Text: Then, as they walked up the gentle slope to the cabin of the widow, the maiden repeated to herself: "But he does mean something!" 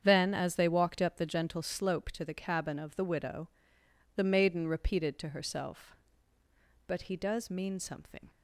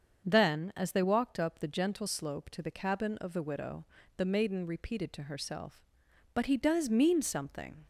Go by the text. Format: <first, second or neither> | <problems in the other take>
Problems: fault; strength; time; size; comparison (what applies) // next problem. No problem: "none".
neither | starts louder than the rest; the same in both